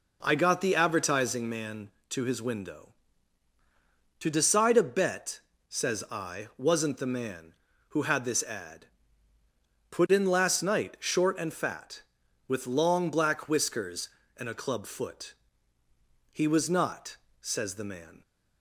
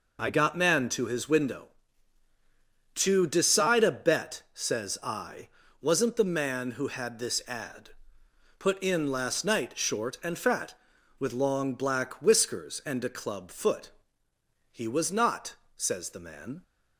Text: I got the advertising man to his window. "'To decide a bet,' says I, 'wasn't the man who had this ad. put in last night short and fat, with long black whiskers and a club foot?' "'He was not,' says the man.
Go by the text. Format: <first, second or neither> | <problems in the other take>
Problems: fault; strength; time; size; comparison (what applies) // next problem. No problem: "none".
first | skips "the advertising"; at 0.5 s